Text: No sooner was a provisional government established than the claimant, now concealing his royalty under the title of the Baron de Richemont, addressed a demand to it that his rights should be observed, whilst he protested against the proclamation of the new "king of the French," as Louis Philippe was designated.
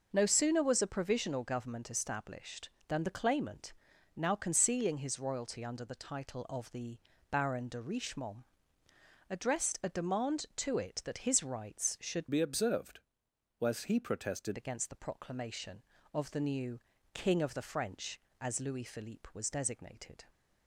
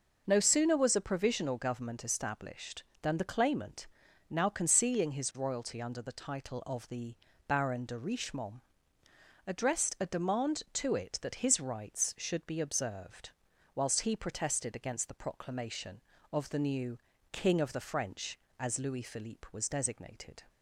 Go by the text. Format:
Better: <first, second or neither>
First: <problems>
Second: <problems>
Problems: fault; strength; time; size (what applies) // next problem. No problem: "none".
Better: second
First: pauses between "the" and "Baron"; slight; at 6.9 s; 0.32 s long // changes voice from "be" to "protested"; from 12.2 to 14.5 s; 2.3 s long // pauses between "new" and "king"; slight; at 16.7 s; 0.36 s long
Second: pauses between "the" and "Baron"; slight; at 7.1 s; 0.32 s long // pauses between "new" and "king"; slight; at 16.9 s; 0.36 s long